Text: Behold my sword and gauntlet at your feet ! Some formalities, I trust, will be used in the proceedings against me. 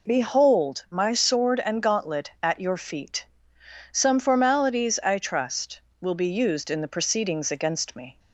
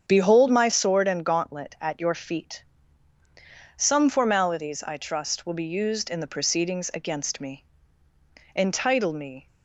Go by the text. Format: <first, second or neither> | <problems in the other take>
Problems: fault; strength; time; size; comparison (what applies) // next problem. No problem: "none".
first | starts louder than the rest; strong; until 1.0 s; 7.5 dB // goes on to say "Entitle me"; noticeable; from 8.5 s on; 0.92 s long